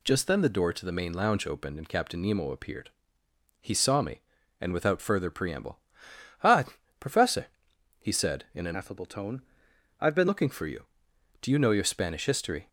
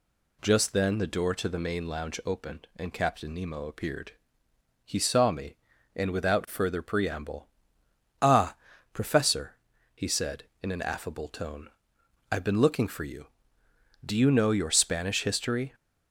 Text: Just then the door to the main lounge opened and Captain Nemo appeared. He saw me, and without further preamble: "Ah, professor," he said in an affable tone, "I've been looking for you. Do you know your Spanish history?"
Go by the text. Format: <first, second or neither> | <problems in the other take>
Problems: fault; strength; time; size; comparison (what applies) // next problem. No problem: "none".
second | changes voice from "affable" to "been"; from 8.7 to 10.2 s; 1.5 s long